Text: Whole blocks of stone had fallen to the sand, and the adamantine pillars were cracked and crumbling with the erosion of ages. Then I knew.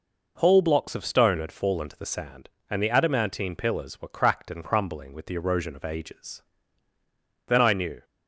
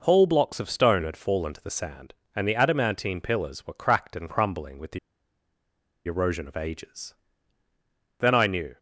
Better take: first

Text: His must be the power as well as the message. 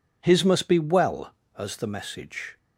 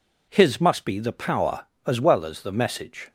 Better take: second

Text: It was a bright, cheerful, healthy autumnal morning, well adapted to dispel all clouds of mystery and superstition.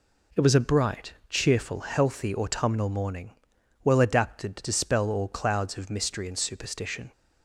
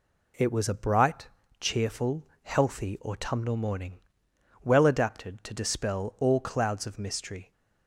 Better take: first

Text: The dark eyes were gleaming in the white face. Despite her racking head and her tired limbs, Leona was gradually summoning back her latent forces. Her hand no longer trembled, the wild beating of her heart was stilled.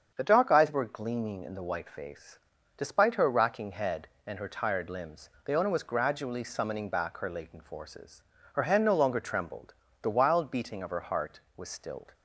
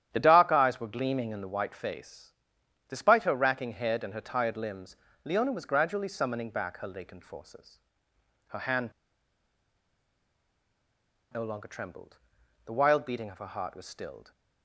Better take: first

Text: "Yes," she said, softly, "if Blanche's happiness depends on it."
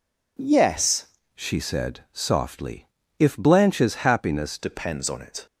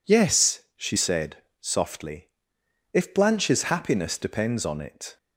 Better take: second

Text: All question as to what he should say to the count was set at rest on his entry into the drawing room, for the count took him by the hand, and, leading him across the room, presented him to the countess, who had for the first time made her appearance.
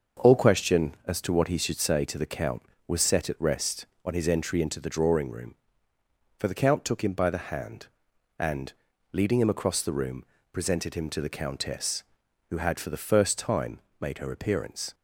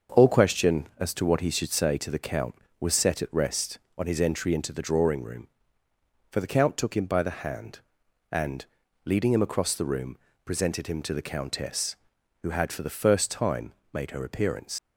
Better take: first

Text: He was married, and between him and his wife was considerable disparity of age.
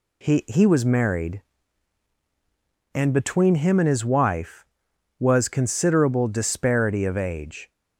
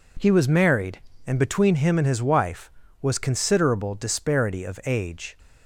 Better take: second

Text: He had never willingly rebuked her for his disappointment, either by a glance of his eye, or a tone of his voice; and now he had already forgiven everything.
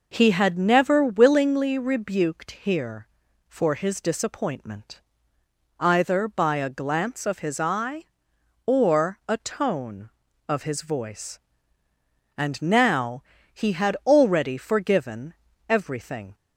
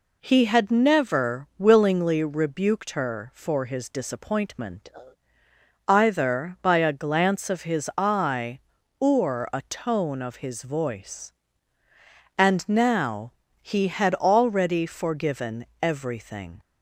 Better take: second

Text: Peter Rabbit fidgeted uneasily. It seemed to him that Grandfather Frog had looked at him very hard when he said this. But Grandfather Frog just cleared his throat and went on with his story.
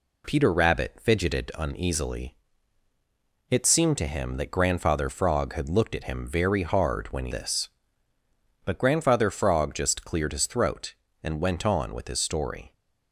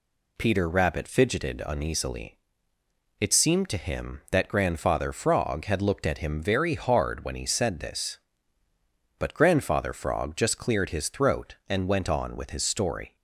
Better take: second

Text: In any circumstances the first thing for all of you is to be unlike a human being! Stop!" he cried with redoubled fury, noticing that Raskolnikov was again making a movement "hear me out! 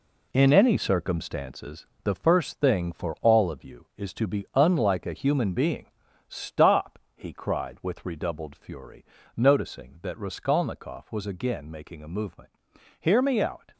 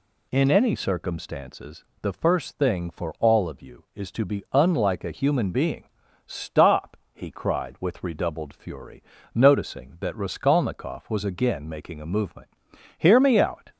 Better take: second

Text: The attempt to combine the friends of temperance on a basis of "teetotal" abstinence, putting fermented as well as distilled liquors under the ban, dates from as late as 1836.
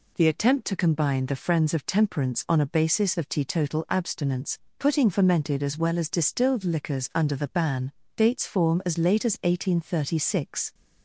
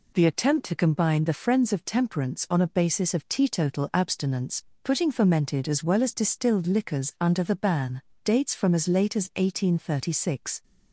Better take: second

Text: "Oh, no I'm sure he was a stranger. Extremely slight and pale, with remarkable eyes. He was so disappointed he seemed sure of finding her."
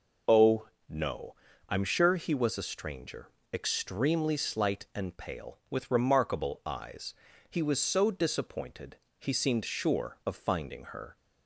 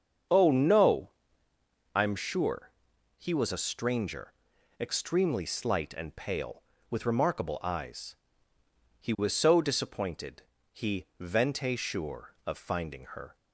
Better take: first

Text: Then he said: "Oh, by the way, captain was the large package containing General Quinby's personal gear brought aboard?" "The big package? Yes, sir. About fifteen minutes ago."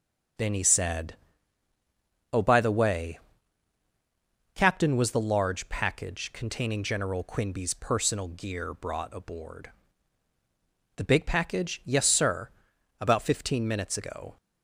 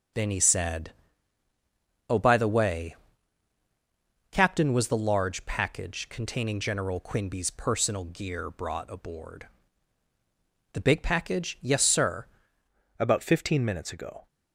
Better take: first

